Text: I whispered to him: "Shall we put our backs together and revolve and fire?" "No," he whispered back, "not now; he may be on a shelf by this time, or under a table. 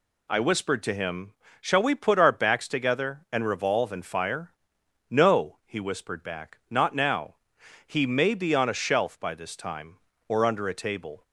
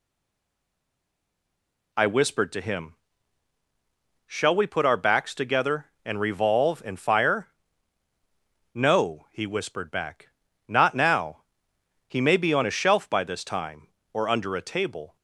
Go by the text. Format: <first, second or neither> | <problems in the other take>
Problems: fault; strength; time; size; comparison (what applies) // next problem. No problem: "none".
first | stays silent before the first word; noticeable; until 1.9 s; 1.9 s long